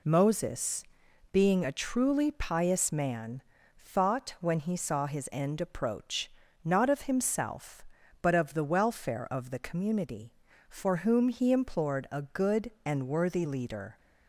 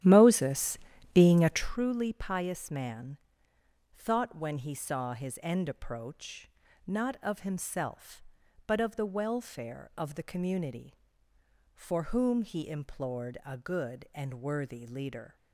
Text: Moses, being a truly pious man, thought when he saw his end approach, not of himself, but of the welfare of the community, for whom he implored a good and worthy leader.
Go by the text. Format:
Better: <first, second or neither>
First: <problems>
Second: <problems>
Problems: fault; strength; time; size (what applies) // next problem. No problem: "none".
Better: first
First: none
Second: starts louder than the rest; strong; until 1.7 s; 11.5 dB